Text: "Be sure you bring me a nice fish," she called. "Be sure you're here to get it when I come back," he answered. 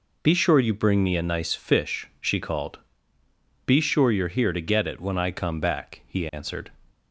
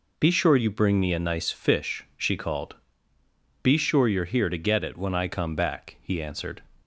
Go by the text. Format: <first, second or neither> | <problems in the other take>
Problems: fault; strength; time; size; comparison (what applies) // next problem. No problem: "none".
neither | none